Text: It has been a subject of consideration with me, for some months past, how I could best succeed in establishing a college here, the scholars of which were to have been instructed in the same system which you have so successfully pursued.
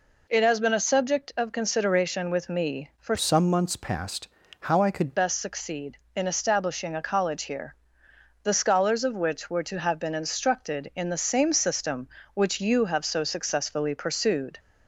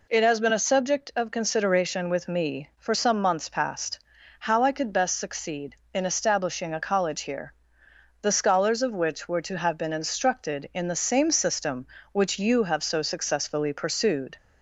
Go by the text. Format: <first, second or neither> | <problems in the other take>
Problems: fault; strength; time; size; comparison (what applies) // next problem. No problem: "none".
second | changes voice from "some" to "could"; from 3.1 to 5.1 s; 2.0 s long